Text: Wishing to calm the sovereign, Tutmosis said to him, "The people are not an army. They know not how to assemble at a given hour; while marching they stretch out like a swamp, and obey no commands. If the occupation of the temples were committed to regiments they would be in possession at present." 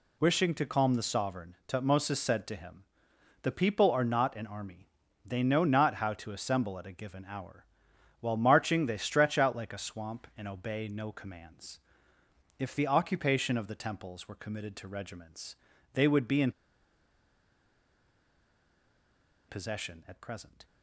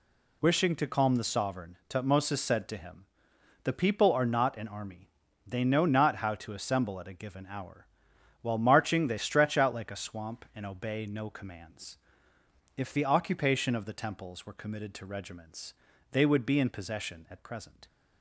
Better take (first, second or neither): second